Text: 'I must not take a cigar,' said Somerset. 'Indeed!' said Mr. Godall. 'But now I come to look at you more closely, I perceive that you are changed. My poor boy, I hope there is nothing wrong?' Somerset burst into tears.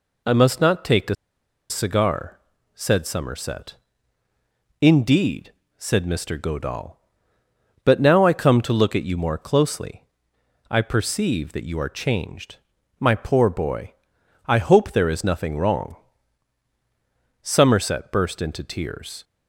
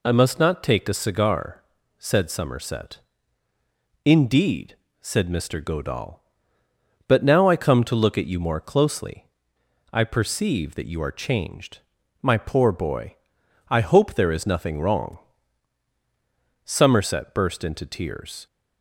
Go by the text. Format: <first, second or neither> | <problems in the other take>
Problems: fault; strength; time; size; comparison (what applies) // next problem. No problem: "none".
second | pauses between "a" and "cigar"; noticeable; at 1.1 s; 0.55 s long